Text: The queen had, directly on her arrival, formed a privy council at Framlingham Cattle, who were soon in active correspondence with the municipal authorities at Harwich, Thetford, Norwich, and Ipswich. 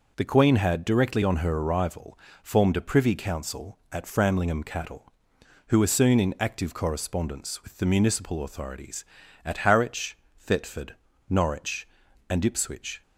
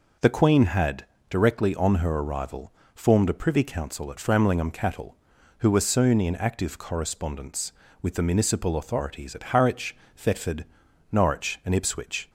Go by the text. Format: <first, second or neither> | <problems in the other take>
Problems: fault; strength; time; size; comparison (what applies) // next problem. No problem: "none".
neither | none